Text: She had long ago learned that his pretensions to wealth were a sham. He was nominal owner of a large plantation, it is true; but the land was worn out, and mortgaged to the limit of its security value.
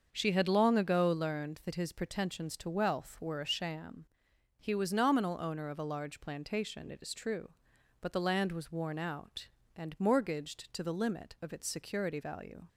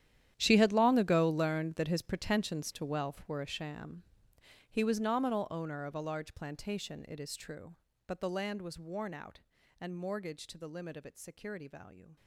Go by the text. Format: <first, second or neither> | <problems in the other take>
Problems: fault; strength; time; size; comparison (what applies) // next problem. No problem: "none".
first | gets quieter; strong; throughout; 17 dB // starts louder than the rest; strong; until 1.3 s; 11 dB; also in the first